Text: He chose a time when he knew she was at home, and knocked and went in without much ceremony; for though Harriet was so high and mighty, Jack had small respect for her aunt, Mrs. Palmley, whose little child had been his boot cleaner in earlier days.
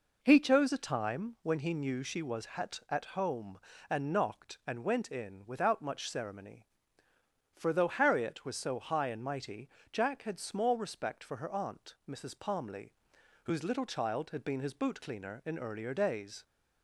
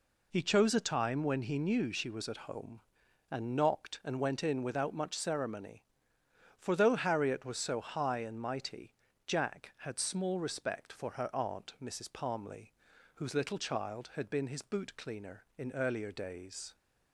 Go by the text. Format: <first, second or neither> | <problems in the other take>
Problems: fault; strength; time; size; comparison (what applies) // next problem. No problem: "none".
second | says "at" twice; at 2.8 s